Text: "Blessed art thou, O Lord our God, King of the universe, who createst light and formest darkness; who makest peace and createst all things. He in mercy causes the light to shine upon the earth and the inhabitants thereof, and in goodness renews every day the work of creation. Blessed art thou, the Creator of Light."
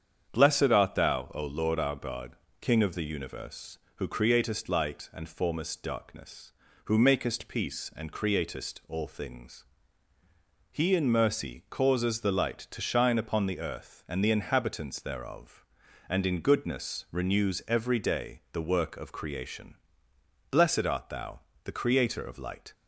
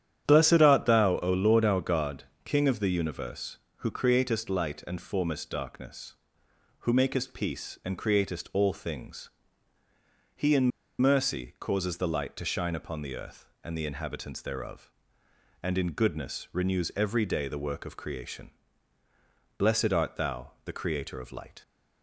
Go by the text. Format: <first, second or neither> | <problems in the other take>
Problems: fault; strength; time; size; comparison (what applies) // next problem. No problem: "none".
first | starts louder than the rest; strong; until 1.2 s; 10 dB; strong in the first // pauses between "in" and "mercy"; slight; at 10.7 s; 0.29 s long